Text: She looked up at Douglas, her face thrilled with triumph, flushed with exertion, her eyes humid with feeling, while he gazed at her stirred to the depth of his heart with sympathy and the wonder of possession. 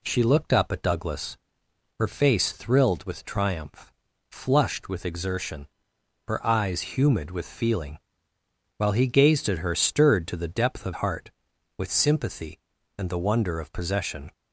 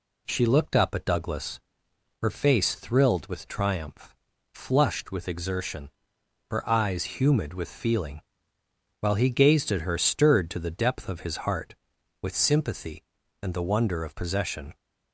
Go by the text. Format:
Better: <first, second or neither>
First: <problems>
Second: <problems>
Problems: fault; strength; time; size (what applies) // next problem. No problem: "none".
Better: second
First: skips "his"; at 10.9 s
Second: none